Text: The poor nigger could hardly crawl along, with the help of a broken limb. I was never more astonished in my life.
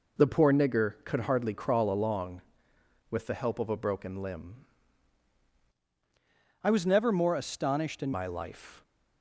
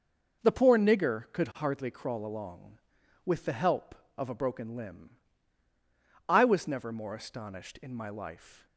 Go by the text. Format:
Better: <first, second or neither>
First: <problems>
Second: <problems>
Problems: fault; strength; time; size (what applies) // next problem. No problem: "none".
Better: second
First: changes voice from "I" to "in"; from 6.6 to 8.1 s; 1.5 s long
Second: none